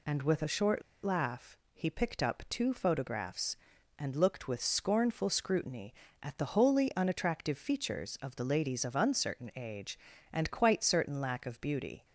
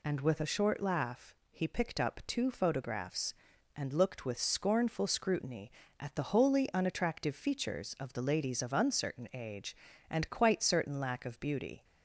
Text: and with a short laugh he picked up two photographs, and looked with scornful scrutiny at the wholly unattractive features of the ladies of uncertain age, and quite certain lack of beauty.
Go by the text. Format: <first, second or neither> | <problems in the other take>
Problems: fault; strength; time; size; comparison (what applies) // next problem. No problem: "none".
second | pauses between "short" and "laugh"; slight; at 0.8 s; 0.22 s long // pauses between "laugh" and "he"; slight; at 1.5 s; 0.18 s long; slight in the second